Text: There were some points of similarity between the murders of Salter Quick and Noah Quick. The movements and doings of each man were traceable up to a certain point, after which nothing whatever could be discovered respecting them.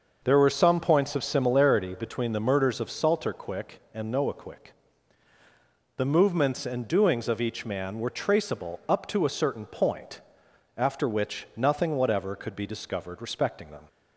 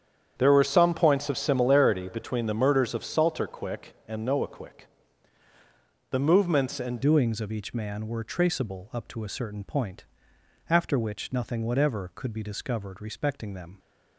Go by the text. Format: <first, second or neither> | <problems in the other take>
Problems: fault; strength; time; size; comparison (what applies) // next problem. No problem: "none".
first | starts louder than the rest; strong; until 1.3 s; 8.5 dB; noticeable in the first // changes voice at "doings"; from 7.0 s on; 6.7 s long